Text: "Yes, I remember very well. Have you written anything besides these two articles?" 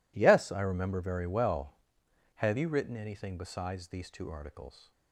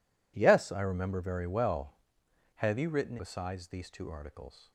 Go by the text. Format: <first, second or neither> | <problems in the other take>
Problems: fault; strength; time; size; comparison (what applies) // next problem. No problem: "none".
first | skips "anything"; at 3.1 s